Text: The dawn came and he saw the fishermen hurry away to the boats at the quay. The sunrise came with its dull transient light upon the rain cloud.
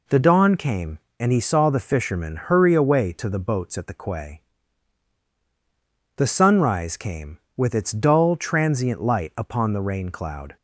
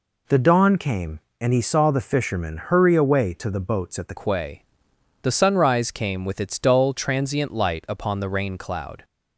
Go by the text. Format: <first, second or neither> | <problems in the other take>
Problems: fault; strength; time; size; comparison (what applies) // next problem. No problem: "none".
first | changes voice at "quay"; from 4.1 s on; 4.9 s long